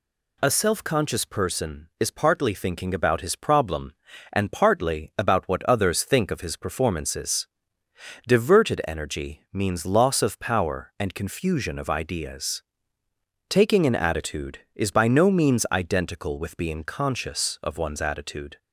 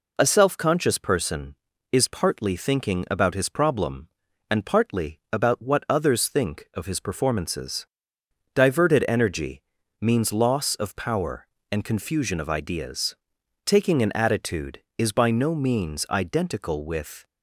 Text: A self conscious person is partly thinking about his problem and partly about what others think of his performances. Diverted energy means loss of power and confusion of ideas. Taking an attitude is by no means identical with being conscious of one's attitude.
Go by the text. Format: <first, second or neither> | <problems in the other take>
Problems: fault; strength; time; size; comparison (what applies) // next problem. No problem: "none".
first | pauses between "energy" and "means"; at 9.6 s; 0.40 s long // stops before "being conscious of one's attitude"; at 17.2 s